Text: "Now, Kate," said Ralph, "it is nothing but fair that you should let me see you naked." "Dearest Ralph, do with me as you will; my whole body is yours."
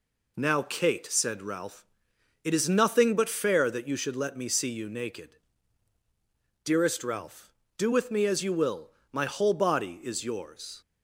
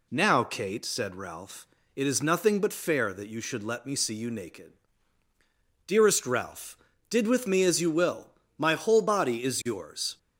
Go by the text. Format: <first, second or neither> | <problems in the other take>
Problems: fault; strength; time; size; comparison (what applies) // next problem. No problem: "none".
first | says "did" for "do"; at 7.1 s